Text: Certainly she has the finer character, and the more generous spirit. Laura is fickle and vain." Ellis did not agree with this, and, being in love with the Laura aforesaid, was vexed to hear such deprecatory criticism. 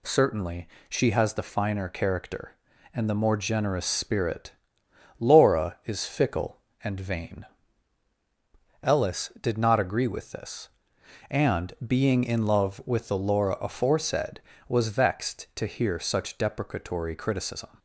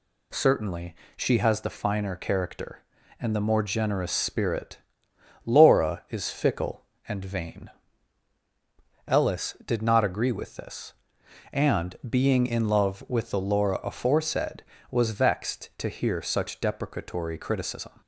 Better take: neither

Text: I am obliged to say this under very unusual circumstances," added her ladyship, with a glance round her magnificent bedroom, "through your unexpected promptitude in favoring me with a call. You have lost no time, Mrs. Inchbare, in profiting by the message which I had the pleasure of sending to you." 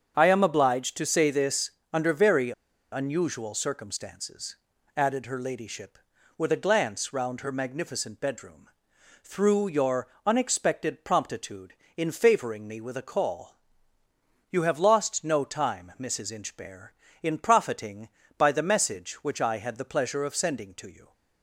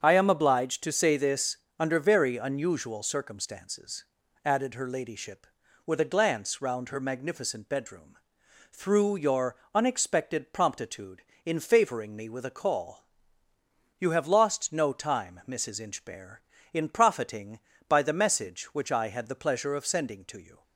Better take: second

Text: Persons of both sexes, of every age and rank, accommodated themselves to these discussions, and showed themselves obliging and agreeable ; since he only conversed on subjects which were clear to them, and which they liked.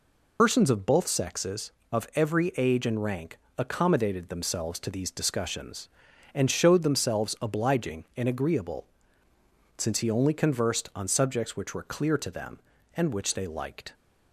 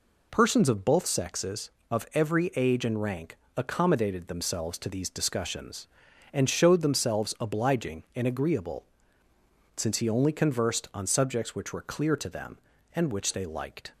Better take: second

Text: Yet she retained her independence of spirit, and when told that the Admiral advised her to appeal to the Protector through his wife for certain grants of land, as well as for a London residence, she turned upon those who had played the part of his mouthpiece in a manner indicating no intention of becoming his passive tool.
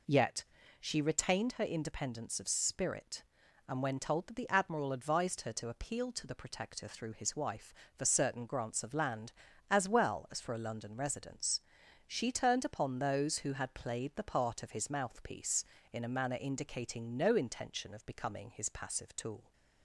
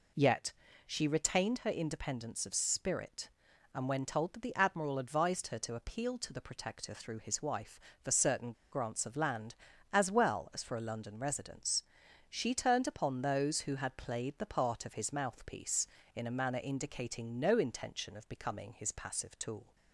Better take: first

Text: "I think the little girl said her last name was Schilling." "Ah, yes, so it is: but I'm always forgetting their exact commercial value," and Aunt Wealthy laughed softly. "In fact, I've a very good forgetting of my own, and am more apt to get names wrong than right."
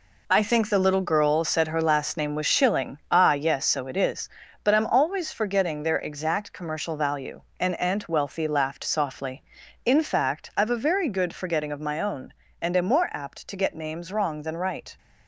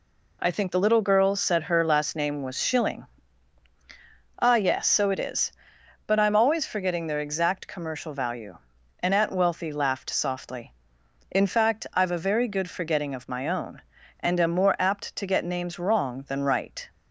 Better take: second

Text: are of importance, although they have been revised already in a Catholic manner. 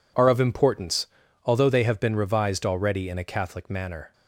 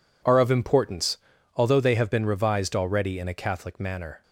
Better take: neither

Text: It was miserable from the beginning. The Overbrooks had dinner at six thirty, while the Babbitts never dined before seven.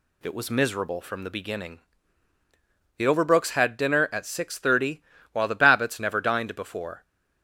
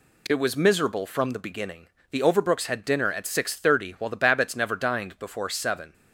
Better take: second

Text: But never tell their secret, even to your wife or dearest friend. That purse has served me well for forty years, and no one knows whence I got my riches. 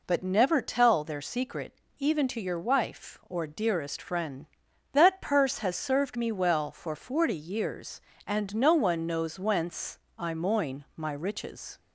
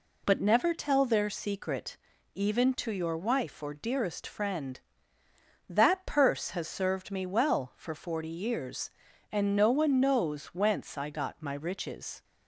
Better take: second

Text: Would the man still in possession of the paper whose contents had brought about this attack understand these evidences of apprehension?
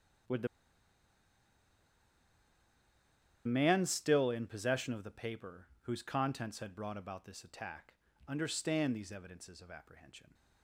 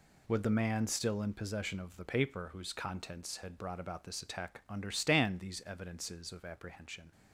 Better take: second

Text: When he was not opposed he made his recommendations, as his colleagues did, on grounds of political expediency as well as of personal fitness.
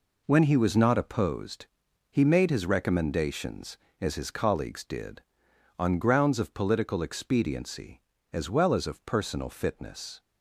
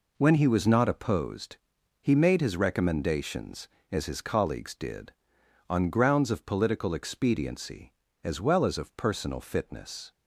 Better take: neither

